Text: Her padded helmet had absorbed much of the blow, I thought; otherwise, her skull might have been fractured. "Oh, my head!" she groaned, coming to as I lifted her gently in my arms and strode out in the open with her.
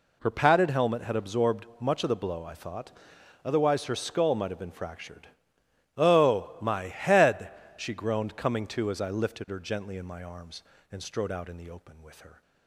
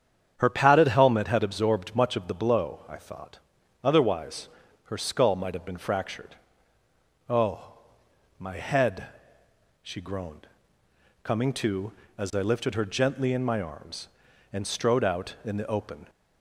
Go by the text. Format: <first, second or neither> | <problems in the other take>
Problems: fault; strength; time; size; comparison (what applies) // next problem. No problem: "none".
first | starts louder than the rest; strong; until 1.3 s; 8.5 dB // stops before "with her"; at 16.0 s